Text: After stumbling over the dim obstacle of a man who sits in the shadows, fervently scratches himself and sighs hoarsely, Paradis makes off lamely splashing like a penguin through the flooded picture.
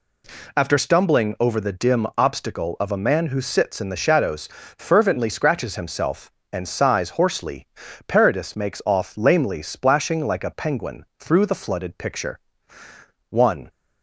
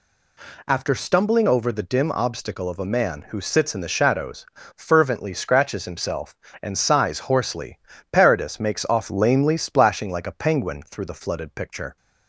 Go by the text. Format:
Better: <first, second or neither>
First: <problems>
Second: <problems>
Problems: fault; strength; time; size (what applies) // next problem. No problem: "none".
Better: second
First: pauses between "penguin" and "through"; slight; at 11.0 s; 0.16 s long // goes on to say "One"; slight; from 13.2 s on; 0.42 s long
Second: none